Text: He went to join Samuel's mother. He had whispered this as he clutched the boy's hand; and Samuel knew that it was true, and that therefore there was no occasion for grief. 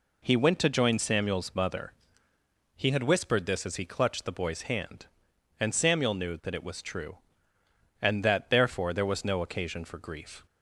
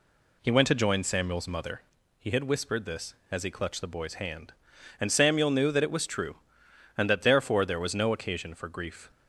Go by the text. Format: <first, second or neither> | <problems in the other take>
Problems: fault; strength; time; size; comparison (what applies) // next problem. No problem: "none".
neither | none